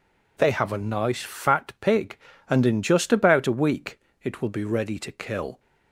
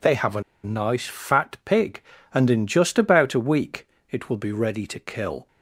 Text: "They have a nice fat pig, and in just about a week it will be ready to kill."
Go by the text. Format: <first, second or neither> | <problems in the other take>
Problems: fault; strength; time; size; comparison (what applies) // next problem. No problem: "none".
first | pauses between "a" and "nice"; slight; at 0.4 s; 0.23 s long // pauses between "week" and "it"; slight; at 3.8 s; 0.24 s long; slight in the first